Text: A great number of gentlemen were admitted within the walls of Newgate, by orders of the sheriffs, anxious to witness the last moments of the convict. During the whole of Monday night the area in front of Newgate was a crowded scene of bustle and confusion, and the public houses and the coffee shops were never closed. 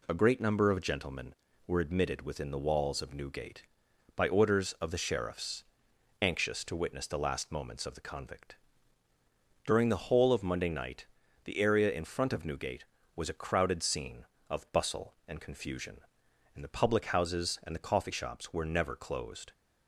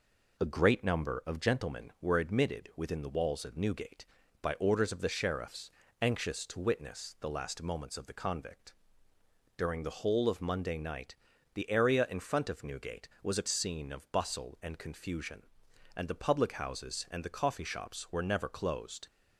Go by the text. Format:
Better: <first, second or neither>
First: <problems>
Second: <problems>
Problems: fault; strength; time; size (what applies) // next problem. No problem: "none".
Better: first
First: pauses between "night" and "the"; at 11.0 s; 0.38 s long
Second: pauses between "night" and "the"; at 11.1 s; 0.40 s long // skips "crowded"; at 13.4 s